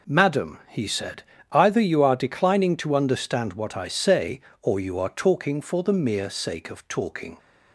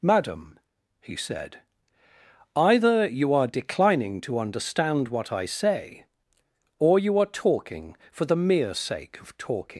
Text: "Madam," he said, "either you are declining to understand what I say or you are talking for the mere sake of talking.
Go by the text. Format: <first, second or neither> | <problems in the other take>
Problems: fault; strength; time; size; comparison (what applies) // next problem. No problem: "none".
first | leaves "talking" unfinished; at 9.7 s; 145 ms